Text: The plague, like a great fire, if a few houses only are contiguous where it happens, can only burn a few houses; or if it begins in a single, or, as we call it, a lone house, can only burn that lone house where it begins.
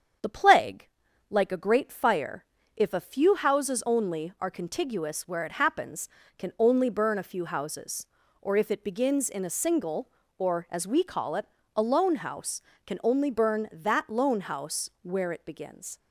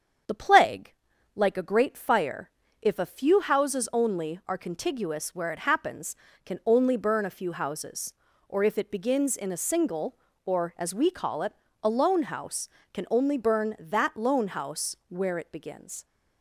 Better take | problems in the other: neither | starts louder than the rest; strong; the same in both

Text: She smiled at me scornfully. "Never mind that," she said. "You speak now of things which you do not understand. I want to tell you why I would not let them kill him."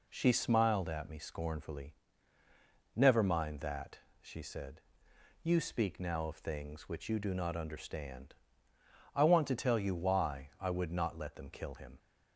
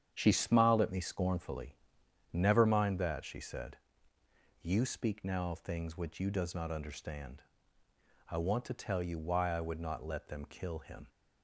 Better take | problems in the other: first | starts louder than the rest; strong; until 1.1 s; 8 dB // says "does" for "do"; at 6.2 s

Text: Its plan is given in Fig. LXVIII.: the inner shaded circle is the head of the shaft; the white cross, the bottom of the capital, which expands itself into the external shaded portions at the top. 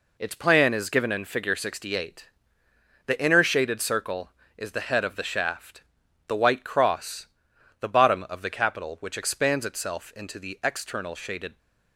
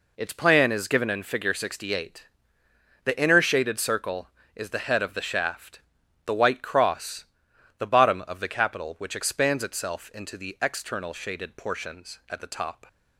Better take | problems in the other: second | stops before "portions at the top"; at 11.5 s

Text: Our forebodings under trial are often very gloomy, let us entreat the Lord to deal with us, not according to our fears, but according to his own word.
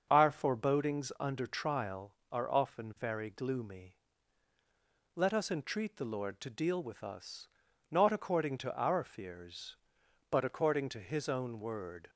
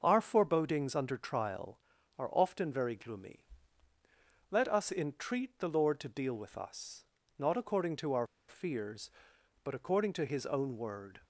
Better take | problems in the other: first | starts louder than the rest; noticeable; until 1.0 s; 6 dB; also in the first // pauses between "our" and "fears"; slight; at 8.2 s; 0.22 s long

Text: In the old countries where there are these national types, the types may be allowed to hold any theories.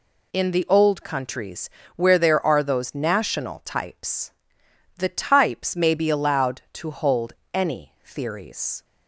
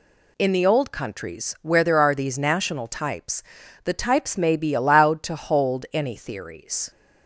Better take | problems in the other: second | pauses between "countries" and "where"; slight; at 1.6 s; 0.26 s long // says "those" for "these"; at 2.6 s // pauses between "hold" and "any"; slight; at 7.3 s; 0.20 s long

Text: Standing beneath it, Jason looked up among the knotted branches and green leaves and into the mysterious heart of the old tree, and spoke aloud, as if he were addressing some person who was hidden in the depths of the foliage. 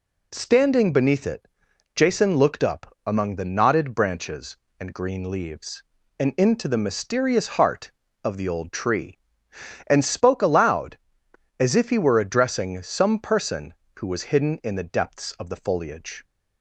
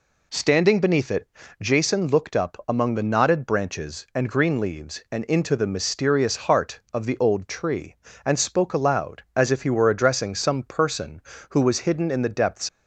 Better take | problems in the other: first | stops before "of the foliage"; at 12.6 s

